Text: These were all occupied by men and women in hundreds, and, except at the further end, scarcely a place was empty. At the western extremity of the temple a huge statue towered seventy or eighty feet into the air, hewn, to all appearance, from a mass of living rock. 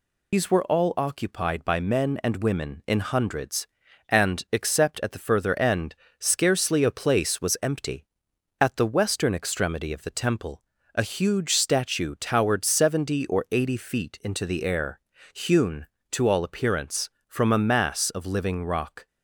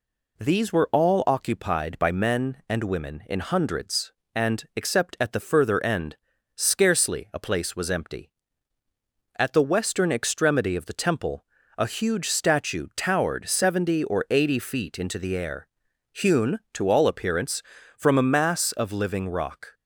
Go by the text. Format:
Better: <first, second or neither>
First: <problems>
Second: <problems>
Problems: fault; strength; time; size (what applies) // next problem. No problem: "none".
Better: second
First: loses the start of "These"; at 0.3 s; 100 ms // pauses between "temple" and "a"; slight; at 10.6 s; 0.32 s long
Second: pauses between "temple" and "a"; slight; at 11.4 s; 0.34 s long